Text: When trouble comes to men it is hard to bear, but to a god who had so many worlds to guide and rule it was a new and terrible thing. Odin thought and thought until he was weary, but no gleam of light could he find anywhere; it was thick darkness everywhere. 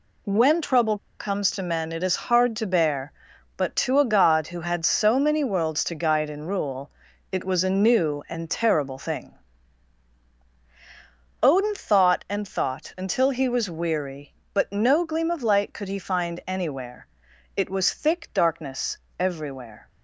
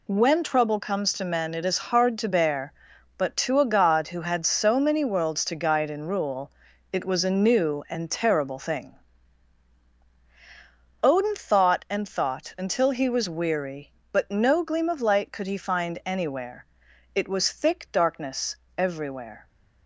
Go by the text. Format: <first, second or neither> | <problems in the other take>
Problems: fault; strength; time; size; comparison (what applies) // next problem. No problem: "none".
second | pauses between "trouble" and "comes"; slight; at 0.9 s; 0.21 s long // pauses between "rule" and "it"; at 6.9 s; 0.40 s long; also in the second // pauses between "darkness" and "everywhere"; slight; at 18.9 s; 0.20 s long; slight in the second